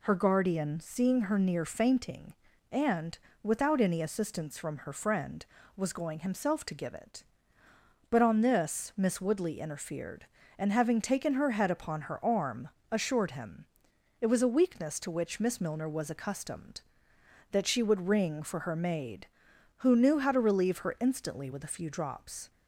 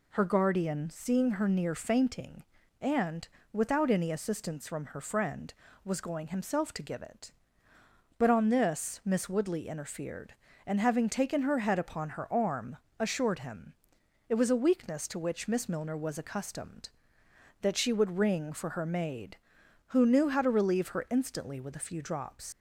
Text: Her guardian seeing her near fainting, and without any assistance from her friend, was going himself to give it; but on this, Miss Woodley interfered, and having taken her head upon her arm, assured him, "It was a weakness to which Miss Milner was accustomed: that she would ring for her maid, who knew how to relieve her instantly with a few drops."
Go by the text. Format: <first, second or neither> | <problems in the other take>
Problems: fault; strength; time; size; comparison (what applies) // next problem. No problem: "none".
first | pauses between "and" and "without"; slight; at 3.2 s; 0.28 s long; slight in the first // leaves "drops" unfinished; at 22.5 s; 95 ms